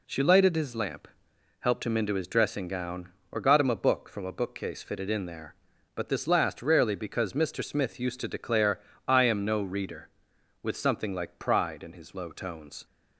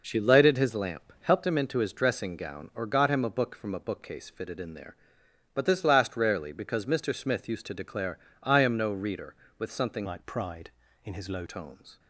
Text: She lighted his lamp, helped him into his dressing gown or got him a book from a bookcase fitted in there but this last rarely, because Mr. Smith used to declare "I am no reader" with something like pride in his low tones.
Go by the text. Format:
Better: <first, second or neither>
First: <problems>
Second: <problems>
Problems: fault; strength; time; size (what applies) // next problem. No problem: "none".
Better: first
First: pauses between "declare" and "I"; slight; at 8.8 s; 0.26 s long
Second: pauses between "declare" and "I"; slight; at 8.1 s; 0.24 s long // changes voice from "like" to "low"; from 10.0 to 11.4 s; 1.4 s long